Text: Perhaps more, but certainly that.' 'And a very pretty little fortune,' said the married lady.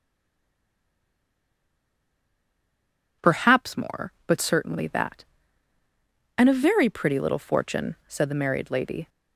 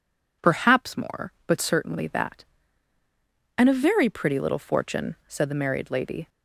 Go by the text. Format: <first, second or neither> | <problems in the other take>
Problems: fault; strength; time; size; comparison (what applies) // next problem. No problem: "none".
second | stays silent before the first word; strong; until 3.2 s; 3.2 s long